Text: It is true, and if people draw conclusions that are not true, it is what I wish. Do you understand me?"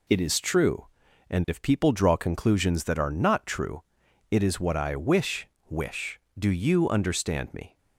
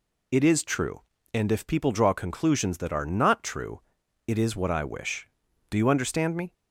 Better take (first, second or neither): second